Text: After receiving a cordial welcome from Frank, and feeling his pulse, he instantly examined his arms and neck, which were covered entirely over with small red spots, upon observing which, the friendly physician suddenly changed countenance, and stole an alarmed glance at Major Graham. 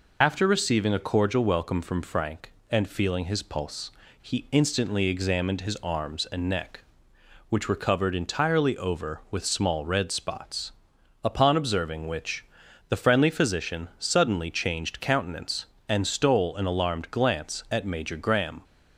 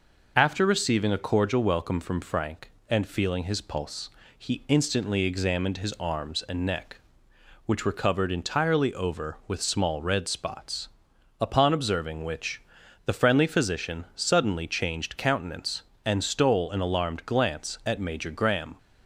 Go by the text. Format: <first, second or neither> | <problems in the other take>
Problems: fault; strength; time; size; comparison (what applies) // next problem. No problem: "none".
second | loses the start of "After"; at 0.2 s; 30 ms